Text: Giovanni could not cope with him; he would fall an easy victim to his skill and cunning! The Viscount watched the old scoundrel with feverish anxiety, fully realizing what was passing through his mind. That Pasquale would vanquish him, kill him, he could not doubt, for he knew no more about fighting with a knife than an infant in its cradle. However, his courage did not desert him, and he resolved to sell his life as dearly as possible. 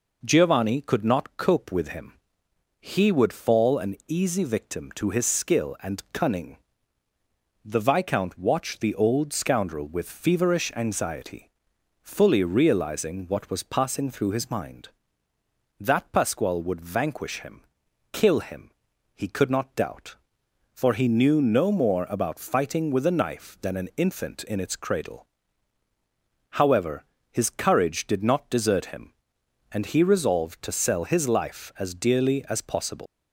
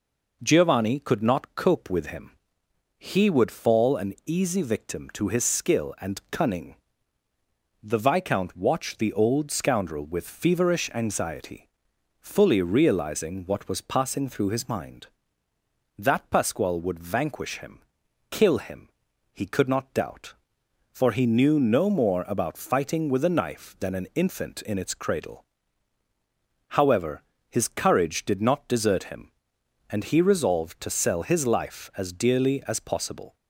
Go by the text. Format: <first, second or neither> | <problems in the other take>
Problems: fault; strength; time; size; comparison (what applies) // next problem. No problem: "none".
second | leaves "possible" unfinished; at 33.0 s; 120 ms